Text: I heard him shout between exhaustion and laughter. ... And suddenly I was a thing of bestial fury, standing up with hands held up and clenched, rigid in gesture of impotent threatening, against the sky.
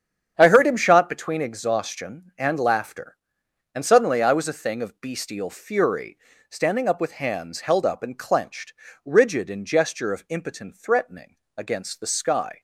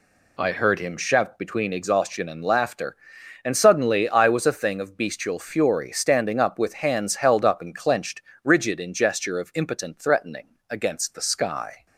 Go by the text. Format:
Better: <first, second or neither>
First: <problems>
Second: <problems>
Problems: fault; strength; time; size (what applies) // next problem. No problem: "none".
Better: second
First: starts louder than the rest; strong; until 1.3 s; 8.5 dB // says "shot" for "shout"; at 0.7 s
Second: none